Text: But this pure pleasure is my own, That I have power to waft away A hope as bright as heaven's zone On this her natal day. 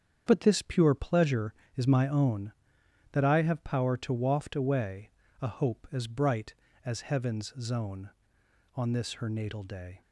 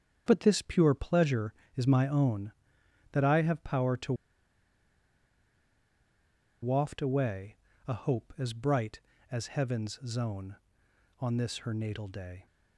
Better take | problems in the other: first | starts louder than the rest; strong; until 1.2 s; 8 dB; strong in the first // pauses between "to" and "waft"; strong; at 4.1 s; 2.4 s long // pauses between "away" and "A"; slight; at 7.5 s; 0.30 s long; slight in the first

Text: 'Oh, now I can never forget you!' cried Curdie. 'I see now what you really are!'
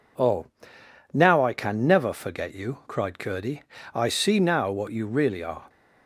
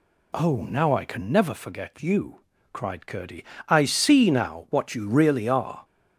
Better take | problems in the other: neither | none

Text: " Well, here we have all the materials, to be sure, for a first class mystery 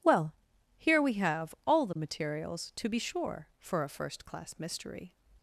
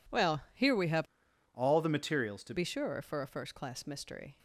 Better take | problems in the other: first | changes voice from "all" to "to"; from 1.5 to 2.5 s; 1.0 s long

